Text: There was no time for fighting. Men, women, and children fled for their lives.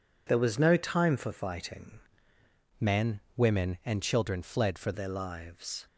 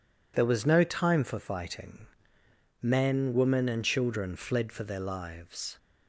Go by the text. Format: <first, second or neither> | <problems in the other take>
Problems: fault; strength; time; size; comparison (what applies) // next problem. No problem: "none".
second | changes voice from "Men" to "for"; from 2.7 to 4.9 s; 2.2 s long